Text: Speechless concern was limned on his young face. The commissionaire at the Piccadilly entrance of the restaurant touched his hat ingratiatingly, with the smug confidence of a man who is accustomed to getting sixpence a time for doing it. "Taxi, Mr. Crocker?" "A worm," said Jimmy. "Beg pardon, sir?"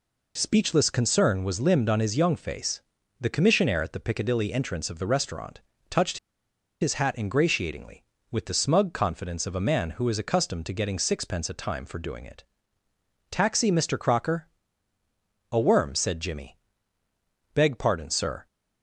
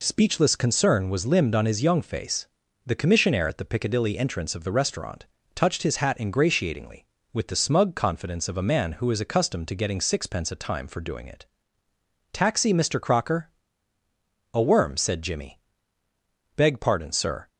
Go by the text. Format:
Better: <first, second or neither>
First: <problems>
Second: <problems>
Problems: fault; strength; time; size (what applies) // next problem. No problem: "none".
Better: second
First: pauses between "restaurant" and "touched"; slight; at 5.6 s; 0.26 s long // pauses between "touched" and "his"; noticeable; at 6.1 s; 0.62 s long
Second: pauses between "restaurant" and "touched"; slight; at 5.2 s; 0.26 s long